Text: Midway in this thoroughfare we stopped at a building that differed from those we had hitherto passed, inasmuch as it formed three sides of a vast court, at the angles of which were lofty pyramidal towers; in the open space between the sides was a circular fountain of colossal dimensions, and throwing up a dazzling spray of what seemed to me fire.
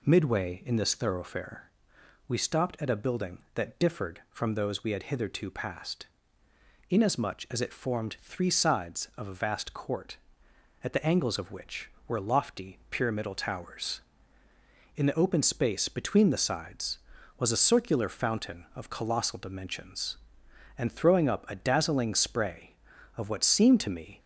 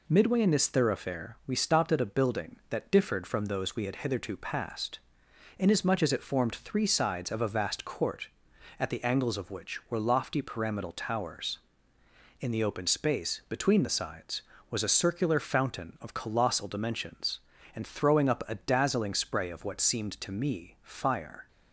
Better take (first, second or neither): second